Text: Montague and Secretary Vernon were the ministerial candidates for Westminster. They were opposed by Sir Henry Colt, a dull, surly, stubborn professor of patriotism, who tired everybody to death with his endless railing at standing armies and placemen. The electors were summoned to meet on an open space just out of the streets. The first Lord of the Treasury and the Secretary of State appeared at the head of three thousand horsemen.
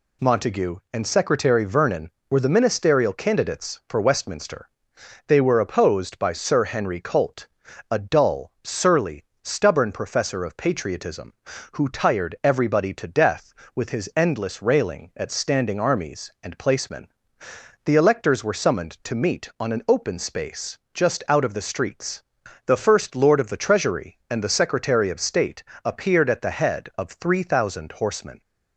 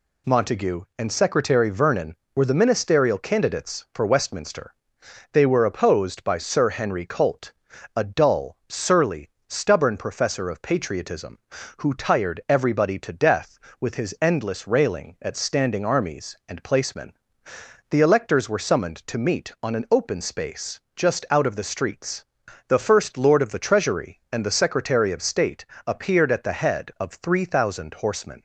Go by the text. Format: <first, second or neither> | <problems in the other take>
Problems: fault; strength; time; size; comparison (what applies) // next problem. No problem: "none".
neither | pauses between "space" and "just"; slight; the same in both // pauses between "State" and "appeared"; slight; the same in both